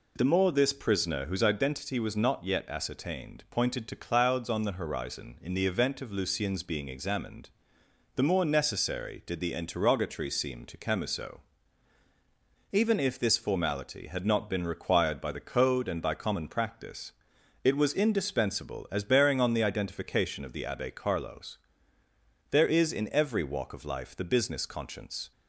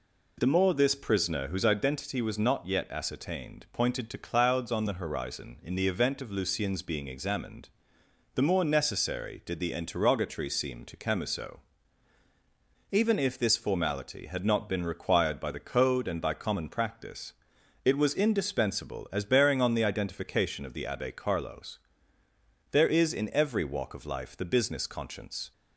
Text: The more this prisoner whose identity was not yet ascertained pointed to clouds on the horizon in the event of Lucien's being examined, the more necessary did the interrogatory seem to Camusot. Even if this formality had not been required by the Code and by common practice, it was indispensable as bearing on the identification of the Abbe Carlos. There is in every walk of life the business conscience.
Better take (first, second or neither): neither